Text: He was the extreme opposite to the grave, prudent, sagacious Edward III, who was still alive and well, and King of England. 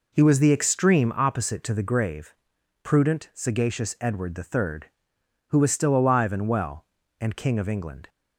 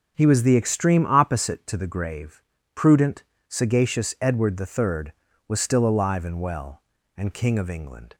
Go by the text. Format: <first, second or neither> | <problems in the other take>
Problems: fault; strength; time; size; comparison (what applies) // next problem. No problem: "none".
first | skips "who"; at 5.2 s